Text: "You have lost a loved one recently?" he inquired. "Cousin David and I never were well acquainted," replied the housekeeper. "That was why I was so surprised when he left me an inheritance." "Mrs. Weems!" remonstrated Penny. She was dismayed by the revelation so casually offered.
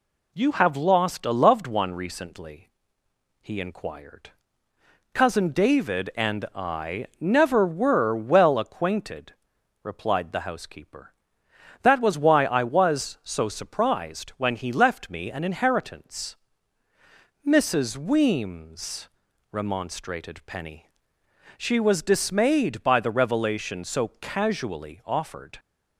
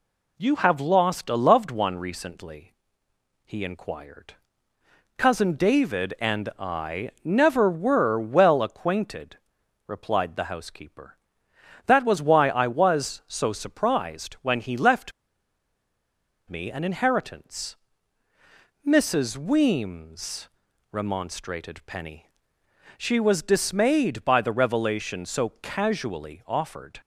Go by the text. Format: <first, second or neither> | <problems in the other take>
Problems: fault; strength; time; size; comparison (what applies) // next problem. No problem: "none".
first | pauses between "left" and "me"; strong; at 15.1 s; 1.3 s long